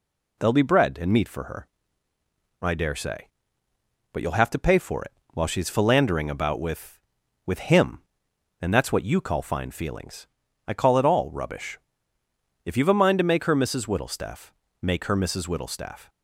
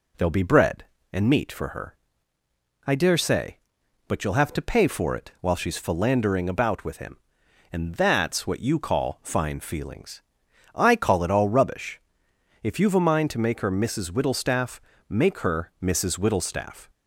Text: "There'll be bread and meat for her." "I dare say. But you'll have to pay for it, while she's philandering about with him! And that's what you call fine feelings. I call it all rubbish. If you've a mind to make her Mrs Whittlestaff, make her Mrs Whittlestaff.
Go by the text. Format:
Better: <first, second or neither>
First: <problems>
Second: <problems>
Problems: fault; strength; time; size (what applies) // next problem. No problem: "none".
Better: second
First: says "with" twice; at 7.4 s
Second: none